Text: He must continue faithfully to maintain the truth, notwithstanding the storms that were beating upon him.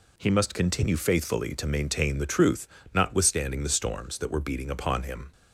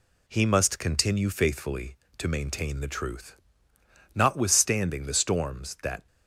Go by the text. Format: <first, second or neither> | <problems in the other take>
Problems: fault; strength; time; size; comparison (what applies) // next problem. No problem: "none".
first | stops before "were beating upon him"; at 6.0 s